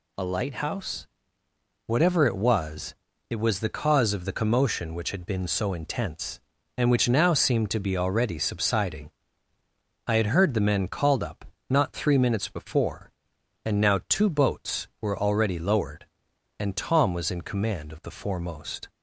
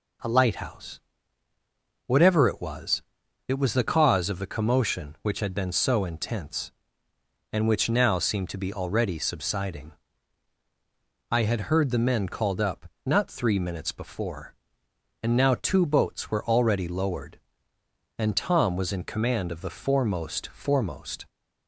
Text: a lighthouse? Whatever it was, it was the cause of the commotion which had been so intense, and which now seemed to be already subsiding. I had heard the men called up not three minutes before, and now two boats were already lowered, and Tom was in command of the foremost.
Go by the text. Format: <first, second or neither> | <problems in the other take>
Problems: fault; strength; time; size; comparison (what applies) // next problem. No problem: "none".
first | pauses between "up" and "not"; slight; at 12.8 s; 0.18 s long; slight in the first // says "foremost" twice; at 20.4 s